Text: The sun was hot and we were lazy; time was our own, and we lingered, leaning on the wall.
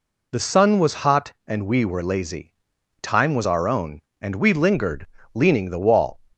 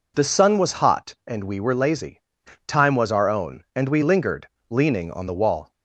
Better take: second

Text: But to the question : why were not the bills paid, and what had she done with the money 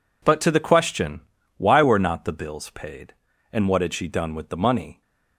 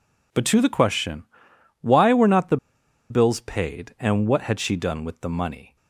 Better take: first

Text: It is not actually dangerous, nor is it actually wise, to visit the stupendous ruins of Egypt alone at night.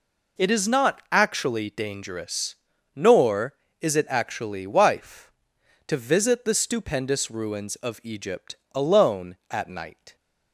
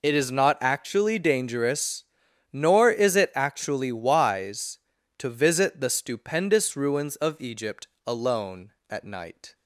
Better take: second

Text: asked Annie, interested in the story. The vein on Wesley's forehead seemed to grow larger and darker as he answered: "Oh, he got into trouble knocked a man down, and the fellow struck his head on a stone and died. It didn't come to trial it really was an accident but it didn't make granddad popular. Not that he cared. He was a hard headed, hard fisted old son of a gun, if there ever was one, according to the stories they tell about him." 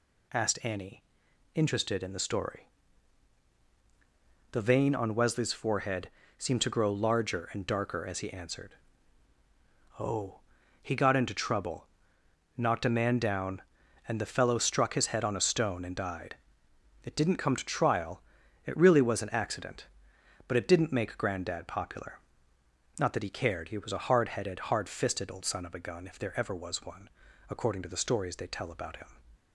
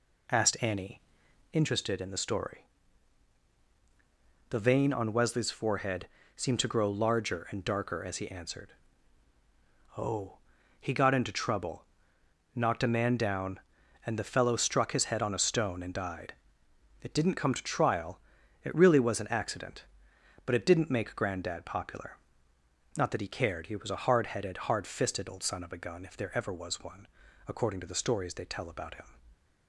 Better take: first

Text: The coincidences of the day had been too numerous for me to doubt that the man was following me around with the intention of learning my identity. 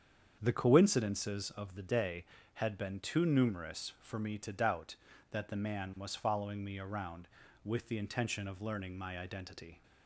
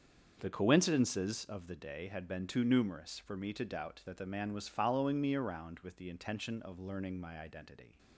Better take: neither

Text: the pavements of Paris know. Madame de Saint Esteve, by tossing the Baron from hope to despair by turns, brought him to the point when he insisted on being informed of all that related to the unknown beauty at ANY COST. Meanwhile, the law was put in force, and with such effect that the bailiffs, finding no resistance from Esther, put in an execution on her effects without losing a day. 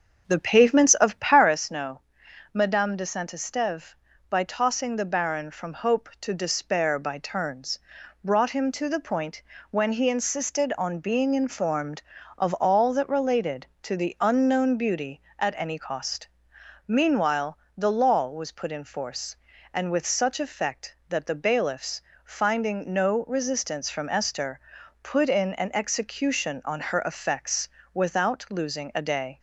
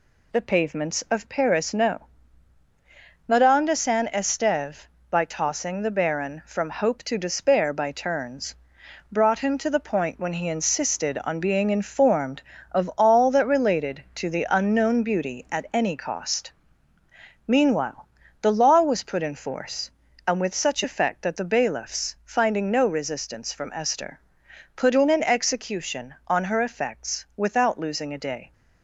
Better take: second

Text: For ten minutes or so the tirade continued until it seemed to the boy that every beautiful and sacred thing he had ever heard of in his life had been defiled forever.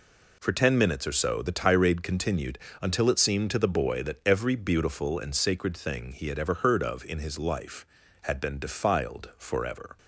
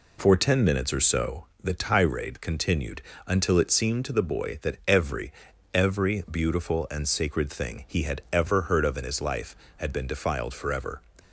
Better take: first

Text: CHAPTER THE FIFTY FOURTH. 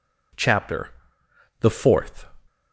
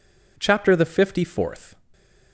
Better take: second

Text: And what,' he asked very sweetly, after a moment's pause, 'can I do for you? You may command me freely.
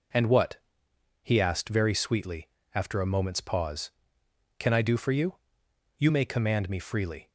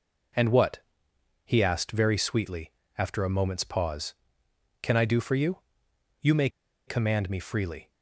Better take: first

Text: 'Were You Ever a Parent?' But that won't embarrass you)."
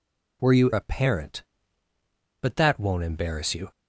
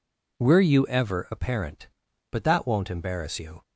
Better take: second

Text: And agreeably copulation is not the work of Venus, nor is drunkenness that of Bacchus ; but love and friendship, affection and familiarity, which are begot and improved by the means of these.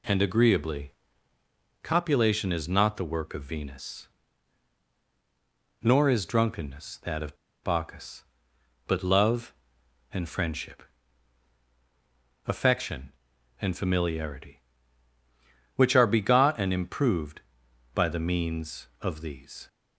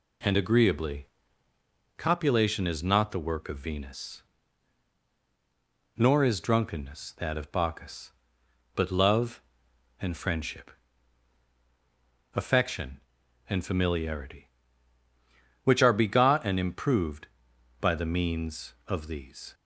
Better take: second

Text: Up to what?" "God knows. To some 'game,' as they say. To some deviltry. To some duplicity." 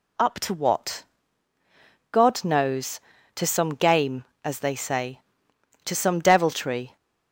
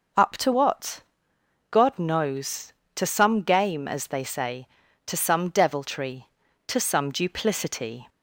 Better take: second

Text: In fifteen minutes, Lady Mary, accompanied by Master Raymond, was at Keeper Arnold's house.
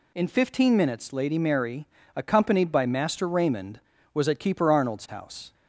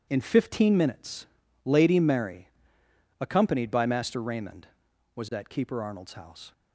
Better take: neither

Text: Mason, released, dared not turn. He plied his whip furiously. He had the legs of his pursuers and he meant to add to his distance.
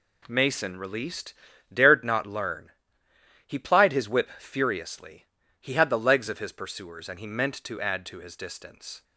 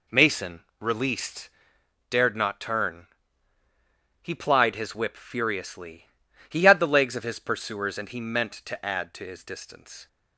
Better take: second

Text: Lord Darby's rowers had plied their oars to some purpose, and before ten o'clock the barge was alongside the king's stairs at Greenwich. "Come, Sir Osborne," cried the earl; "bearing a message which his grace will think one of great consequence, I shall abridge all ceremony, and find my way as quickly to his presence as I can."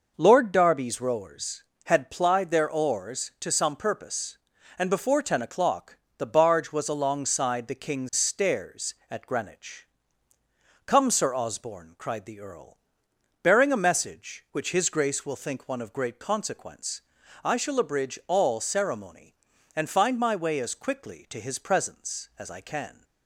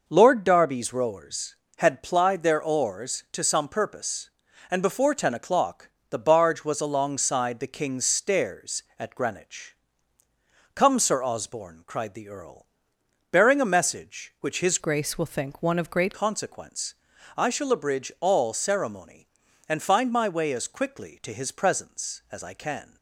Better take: first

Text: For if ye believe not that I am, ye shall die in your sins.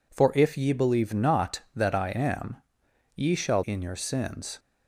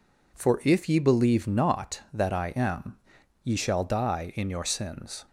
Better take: second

